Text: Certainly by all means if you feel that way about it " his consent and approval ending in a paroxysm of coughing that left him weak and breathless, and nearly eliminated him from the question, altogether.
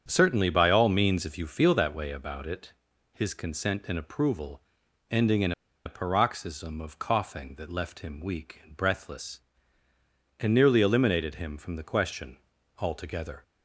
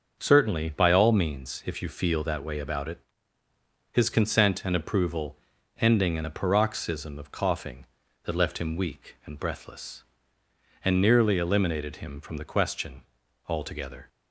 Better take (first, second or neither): second